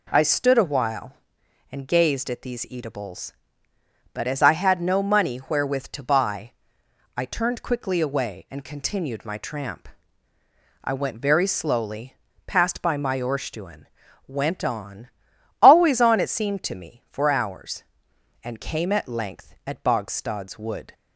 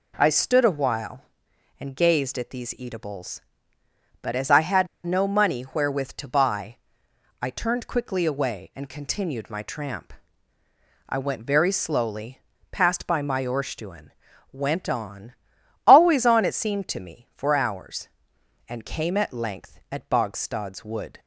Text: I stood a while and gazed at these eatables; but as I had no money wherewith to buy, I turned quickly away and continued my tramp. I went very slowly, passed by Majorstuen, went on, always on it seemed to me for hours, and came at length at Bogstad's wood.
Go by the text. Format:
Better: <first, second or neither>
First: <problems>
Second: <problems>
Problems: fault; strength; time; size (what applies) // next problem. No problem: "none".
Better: first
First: none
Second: pauses between "had" and "no"; slight; at 4.8 s; 0.18 s long